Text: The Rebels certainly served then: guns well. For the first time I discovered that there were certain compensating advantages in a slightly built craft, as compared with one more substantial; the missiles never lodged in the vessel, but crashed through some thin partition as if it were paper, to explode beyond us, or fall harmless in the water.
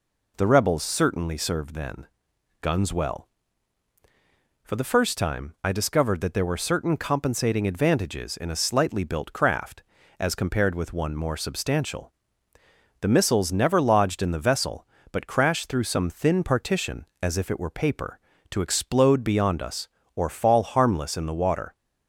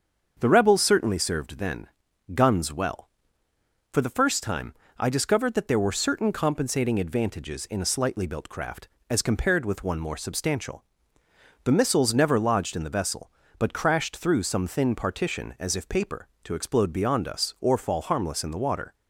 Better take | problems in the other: first | starts louder than the rest; until 1.4 s; 7 dB // pauses between "time" and "I"; slight; at 4.7 s; 0.26 s long // skips "it were"; at 15.8 s

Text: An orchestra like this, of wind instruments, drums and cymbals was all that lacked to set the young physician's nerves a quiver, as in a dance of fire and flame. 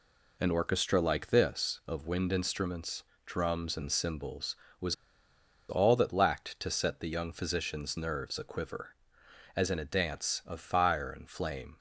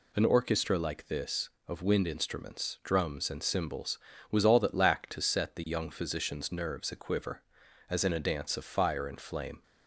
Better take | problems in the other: second | pauses between "was" and "all"; noticeable; at 4.9 s; 0.74 s long

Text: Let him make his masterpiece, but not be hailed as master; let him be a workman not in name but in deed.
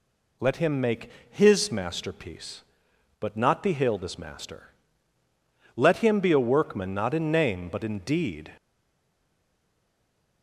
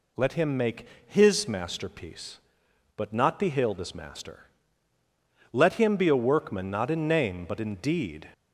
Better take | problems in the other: second | pauses between "make" and "his"; slight; at 1.0 s; 0.20 s long; slight in the second // stays silent after the last word; noticeable; from 8.5 s on; 1.9 s long

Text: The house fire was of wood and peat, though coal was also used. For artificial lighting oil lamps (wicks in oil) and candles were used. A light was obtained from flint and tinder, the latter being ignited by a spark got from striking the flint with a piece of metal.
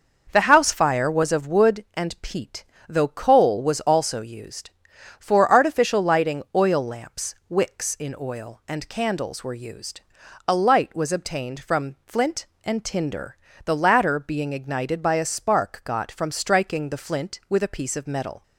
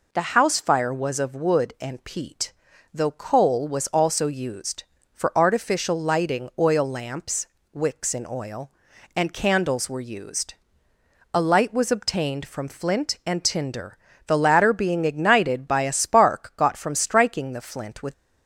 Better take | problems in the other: first | stops before "a piece of metal"; at 18.1 s

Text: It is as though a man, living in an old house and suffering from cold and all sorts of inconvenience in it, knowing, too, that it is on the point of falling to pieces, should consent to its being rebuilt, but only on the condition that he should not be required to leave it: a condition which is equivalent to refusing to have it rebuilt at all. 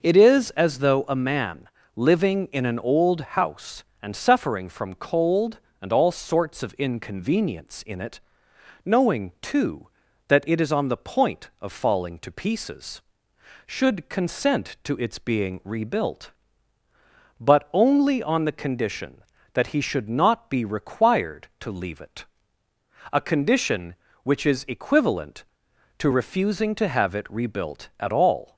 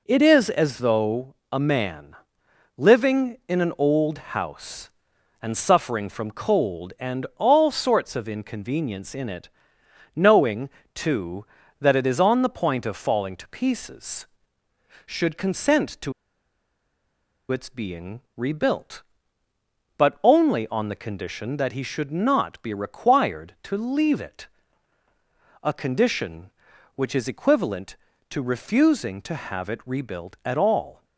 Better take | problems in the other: first | pauses between "though" and "a"; slight; at 1.3 s; 0.16 s long // pauses between "to" and "its"; strong; at 16.1 s; 1.3 s long // pauses between "being" and "rebuilt"; slight; at 18.1 s; 0.16 s long

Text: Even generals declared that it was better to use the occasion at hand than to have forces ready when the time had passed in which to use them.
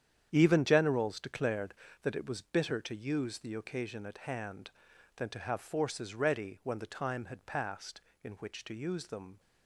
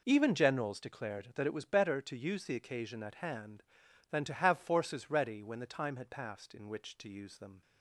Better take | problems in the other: second | starts louder than the rest; strong; until 1.3 s; 9 dB // says "bitter" for "better"; at 2.4 s

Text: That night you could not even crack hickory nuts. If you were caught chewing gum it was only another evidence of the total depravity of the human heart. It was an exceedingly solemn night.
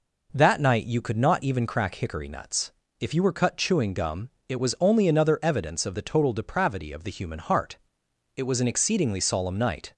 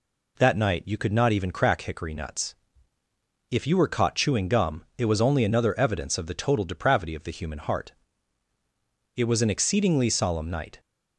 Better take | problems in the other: second | says "cut" for "caught"; at 3.3 s // pauses between "gum" and "it"; slight; at 4.2 s; 0.18 s long

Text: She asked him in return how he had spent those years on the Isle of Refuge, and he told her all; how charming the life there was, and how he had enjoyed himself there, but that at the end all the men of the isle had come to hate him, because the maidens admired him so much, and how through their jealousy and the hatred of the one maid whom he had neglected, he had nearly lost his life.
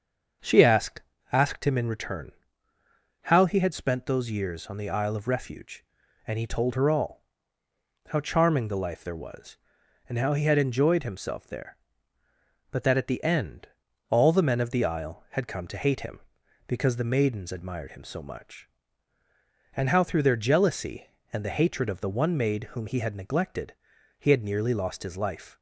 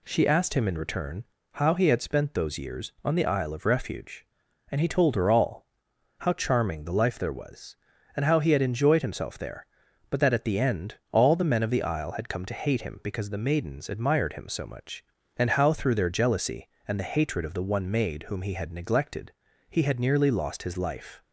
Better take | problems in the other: second | starts louder than the rest; until 1.7 s; 6.5 dB // says "asked" twice; at 1.3 s // pauses between "return" and "how"; noticeable; at 2.3 s; 0.92 s long; slight in the second // pauses between "end" and "all"; at 13.6 s; 0.40 s long; slight in the second

